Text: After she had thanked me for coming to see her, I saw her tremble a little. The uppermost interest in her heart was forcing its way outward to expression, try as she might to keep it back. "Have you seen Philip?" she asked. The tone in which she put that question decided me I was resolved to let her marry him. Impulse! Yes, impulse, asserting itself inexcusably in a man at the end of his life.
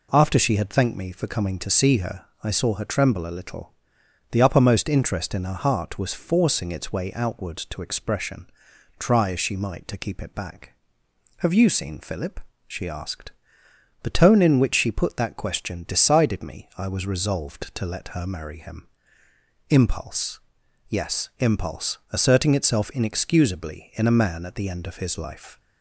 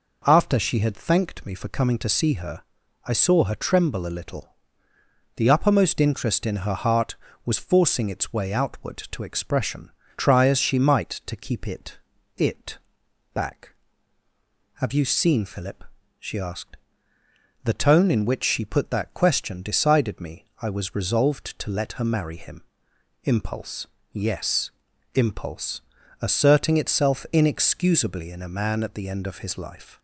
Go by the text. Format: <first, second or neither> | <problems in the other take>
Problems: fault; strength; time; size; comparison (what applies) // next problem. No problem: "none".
first | says "it" twice; at 12.3 s // pauses between "me" and "I"; slight; at 20.4 s; 0.16 s long